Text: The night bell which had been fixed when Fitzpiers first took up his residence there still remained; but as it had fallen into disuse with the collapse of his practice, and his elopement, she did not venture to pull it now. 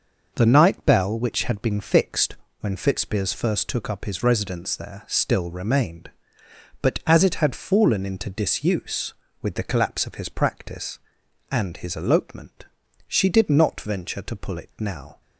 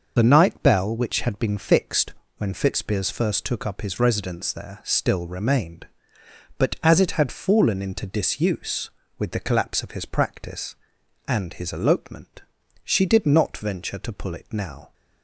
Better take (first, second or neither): first